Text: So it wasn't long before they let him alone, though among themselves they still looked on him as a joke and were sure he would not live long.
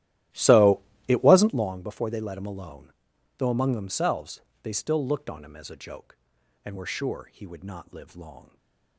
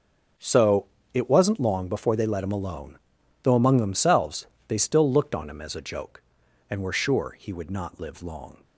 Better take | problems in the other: second | starts louder than the rest; strong; until 1.7 s; 14 dB // pauses between "So" and "it"; slight; at 0.8 s; 0.26 s long; slight in the second // pauses between "themselves" and "they"; slight; at 4.4 s; 0.22 s long; slight in the second // stays silent after the last word; slight; from 8.4 s on; 0.5 s long

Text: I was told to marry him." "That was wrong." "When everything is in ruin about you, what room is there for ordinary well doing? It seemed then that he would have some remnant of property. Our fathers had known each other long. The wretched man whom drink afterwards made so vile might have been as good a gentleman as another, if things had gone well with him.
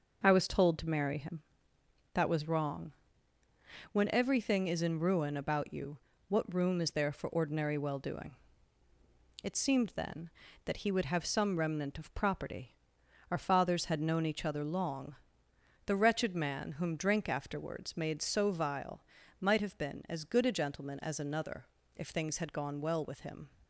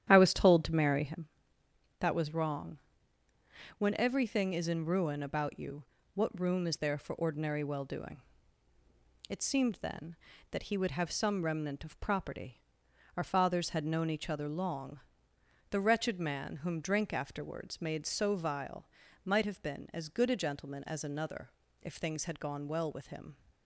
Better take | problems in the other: first | starts louder than the rest; strong; until 1.2 s; 10.5 dB // pauses between "vile" and "might"; at 18.8 s; 0.38 s long; also in the first

